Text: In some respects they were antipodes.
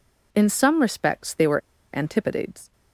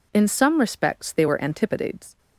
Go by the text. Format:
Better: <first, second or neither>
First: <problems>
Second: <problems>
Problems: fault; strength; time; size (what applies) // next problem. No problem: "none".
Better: second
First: pauses between "were" and "antipodes"; slight; at 1.6 s; 0.35 s long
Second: none